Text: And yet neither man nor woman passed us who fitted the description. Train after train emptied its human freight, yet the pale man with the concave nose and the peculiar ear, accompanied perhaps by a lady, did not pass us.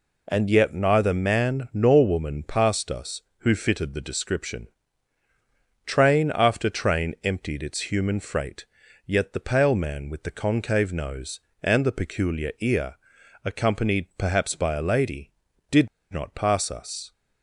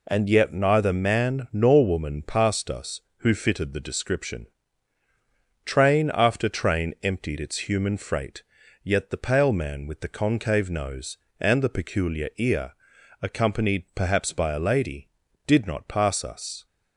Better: second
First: pauses between "did" and "not"; slight; at 15.8 s; 0.24 s long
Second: none

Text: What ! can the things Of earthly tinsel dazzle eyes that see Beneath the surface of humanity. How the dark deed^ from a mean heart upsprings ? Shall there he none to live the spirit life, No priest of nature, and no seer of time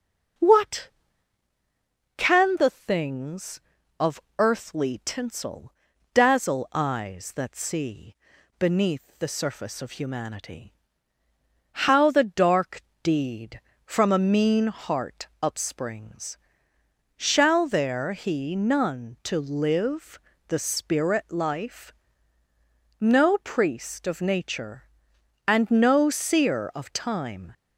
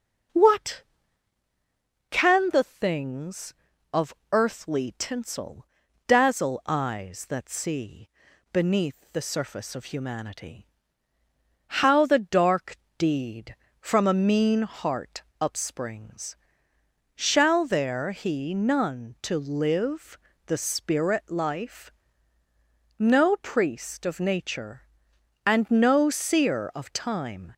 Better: neither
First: starts louder than the rest; until 2.6 s; 6.5 dB // pauses between "Of" and "earthly"; slight; at 4.2 s; 0.18 s long // pauses between "tinsel" and "dazzle"; at 5.7 s; 0.40 s long // pauses between "see" and "Beneath"; at 8.1 s; 0.42 s long // pauses between "dark" and "deed"; slight; at 12.8 s; 0.22 s long // pauses between "heart" and "upsprings"; slight; at 15.2 s; 0.16 s long // pauses between "live" and "the"; slight; at 20.2 s; 0.28 s long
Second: starts louder than the rest; until 2.6 s; 6.5 dB // pauses between "Of" and "earthly"; slight; at 4.1 s; 0.18 s long // pauses between "tinsel" and "dazzle"; at 5.6 s; 0.40 s long // pauses between "see" and "Beneath"; at 8.0 s; 0.42 s long // pauses between "dark" and "deed"; slight; at 12.7 s; 0.22 s long // pauses between "heart" and "upsprings"; slight; at 15.2 s; 0.19 s long // pauses between "live" and "the"; slight; at 20.1 s; 0.28 s long

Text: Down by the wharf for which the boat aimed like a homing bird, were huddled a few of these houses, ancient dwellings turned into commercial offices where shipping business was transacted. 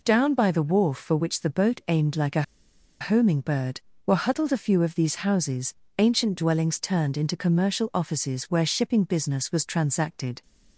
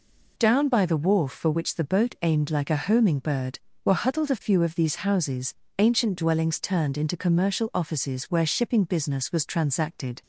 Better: second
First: pauses between "a" and "homing"; noticeable; at 2.4 s; 0.58 s long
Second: none

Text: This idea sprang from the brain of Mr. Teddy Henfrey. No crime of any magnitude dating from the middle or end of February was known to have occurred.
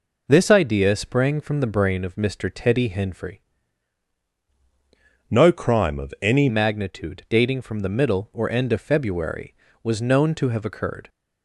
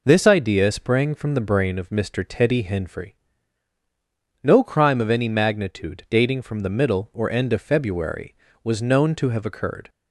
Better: second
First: changes voice from "No" to "any"; from 5.3 to 6.4 s; 1.1 s long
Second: none

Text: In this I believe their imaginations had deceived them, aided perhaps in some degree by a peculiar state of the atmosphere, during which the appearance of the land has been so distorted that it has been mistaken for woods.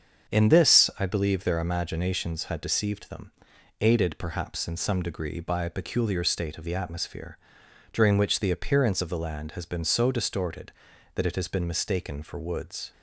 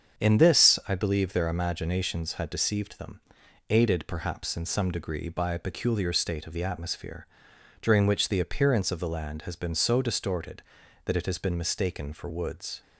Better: neither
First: starts louder than the rest; until 1.3 s; 7 dB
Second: starts louder than the rest; strong; until 1.2 s; 7 dB

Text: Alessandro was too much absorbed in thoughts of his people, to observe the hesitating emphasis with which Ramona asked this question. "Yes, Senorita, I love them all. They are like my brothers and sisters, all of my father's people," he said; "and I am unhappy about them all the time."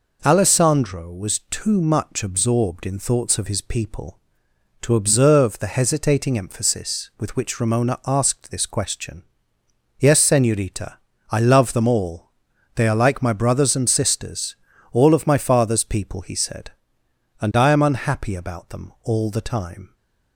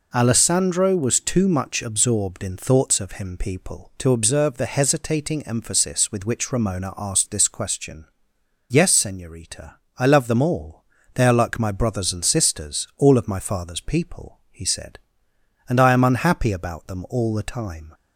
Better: first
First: none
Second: says "him" for "his"; at 3.1 s

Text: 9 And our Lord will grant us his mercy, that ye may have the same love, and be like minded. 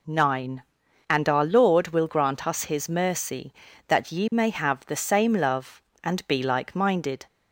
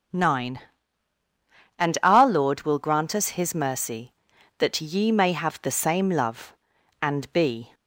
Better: first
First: none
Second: starts louder than the rest; strong; until 2.3 s; 7 dB // stops before "like minded"; at 7.7 s

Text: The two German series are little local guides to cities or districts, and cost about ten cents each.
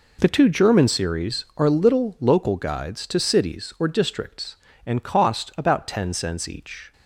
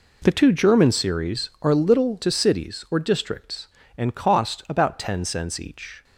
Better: first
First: none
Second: skips "local guides"; at 2.2 s

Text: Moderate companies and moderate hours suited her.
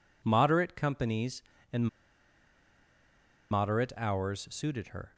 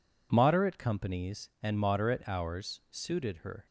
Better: second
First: pauses between "and" and "moderate"; strong; at 1.8 s; 1.6 s long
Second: none

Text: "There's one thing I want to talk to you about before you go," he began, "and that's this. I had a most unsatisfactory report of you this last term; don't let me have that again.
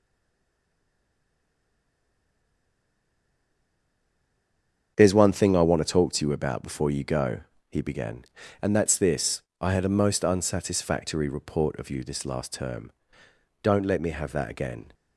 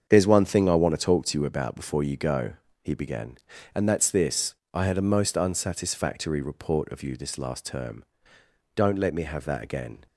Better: second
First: stays silent before the first word; strong; until 4.9 s; 4.9 s long // starts louder than the rest; strong; until 5.9 s; 7.5 dB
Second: starts louder than the rest; strong; until 1.0 s; 7.5 dB

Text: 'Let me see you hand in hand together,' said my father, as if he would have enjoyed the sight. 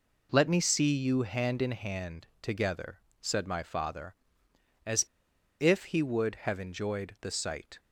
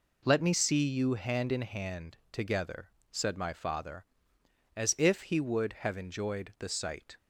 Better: second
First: pauses between "as" and "if"; noticeable; at 5.0 s; 0.56 s long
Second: none

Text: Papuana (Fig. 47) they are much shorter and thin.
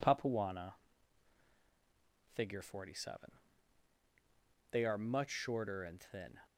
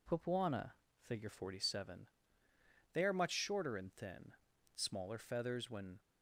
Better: first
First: none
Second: goes on to say "Smaller feathers when"; noticeable; from 4.7 s on; 1.2 s long

